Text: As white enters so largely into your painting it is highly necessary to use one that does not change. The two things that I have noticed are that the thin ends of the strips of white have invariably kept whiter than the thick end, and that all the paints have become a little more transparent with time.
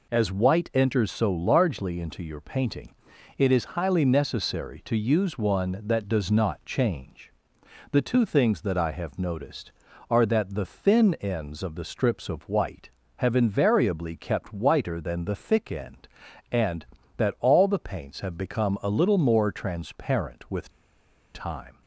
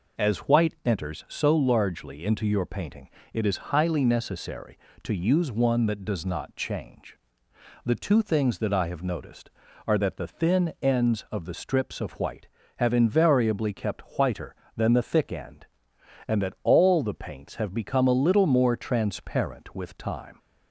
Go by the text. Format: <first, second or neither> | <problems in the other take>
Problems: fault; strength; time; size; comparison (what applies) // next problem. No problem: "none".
second | pauses between "painting" and "it"; at 2.9 s; 0.42 s long; slight in the second // pauses between "with" and "time"; noticeable; at 20.6 s; 0.64 s long